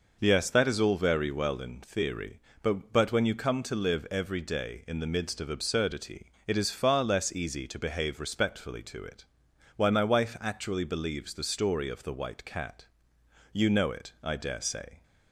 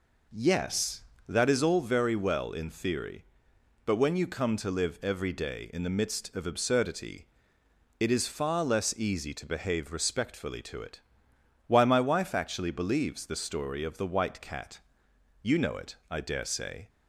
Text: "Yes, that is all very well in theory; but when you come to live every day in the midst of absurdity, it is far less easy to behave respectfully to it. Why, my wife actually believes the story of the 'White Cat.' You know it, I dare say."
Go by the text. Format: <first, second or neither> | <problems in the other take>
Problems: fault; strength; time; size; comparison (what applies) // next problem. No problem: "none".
second | says "but" twice; at 2.9 s